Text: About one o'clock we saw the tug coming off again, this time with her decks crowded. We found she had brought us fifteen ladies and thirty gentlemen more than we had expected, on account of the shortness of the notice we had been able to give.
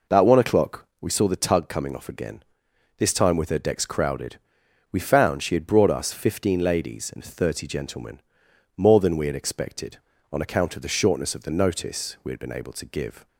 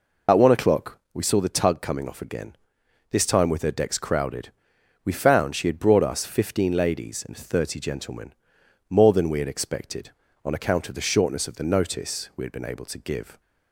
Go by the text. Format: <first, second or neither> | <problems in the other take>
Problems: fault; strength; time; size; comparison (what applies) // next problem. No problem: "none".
first | loses the start of "About"; at 0.2 s; 65 ms // pauses between "o'clock" and "we"; slight; at 0.9 s; 0.16 s long; slight in the first // pauses between "gentlemen" and "more"; noticeable; at 8.3 s; 0.56 s long; noticeable in the first